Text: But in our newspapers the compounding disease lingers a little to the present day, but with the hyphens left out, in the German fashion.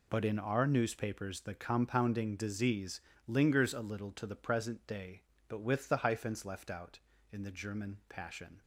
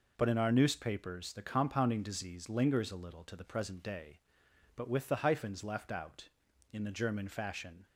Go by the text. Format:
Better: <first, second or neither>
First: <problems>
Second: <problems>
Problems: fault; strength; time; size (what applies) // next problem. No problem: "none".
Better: second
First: pauses between "disease" and "lingers"; slight; at 3.0 s; 0.24 s long // says "passion" for "fashion"; at 8.0 s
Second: none